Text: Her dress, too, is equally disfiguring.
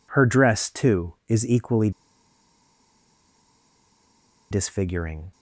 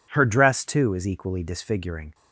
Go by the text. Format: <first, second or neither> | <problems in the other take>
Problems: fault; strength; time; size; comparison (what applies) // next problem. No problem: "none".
second | pauses between "equally" and "disfiguring"; strong; at 1.9 s; 2.5 s long